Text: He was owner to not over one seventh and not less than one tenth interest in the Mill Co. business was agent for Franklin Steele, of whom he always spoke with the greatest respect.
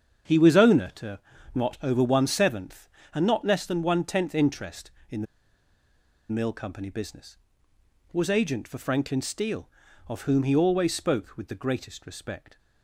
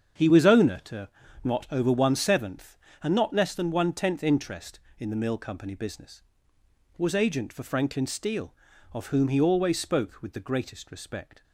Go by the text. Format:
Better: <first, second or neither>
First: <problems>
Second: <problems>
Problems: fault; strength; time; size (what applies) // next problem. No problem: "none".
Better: second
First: starts louder than the rest; strong; until 1.6 s; 8 dB // pauses between "to" and "not"; slight; at 1.2 s; 0.34 s long // pauses between "the" and "Mill"; at 5.2 s; 1.0 s long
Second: starts louder than the rest; strong; until 1.5 s; 8 dB // pauses between "to" and "not"; slight; at 1.0 s; 0.34 s long